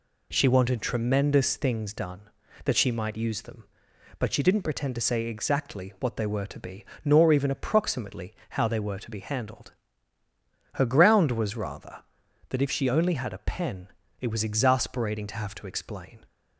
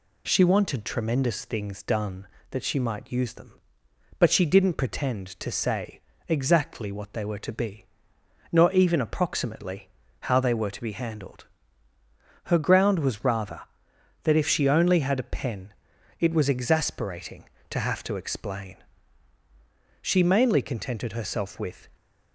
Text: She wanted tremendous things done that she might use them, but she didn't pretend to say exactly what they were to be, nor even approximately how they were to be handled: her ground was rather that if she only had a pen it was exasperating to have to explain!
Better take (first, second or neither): first